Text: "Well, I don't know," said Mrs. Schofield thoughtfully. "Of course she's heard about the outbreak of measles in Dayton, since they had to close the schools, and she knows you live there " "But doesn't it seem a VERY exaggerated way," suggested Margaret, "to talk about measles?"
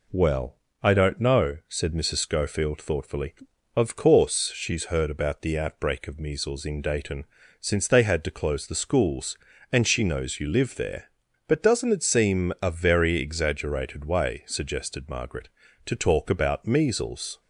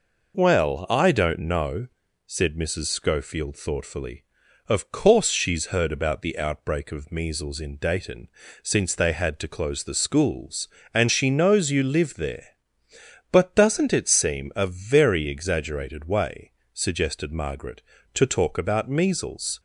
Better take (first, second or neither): neither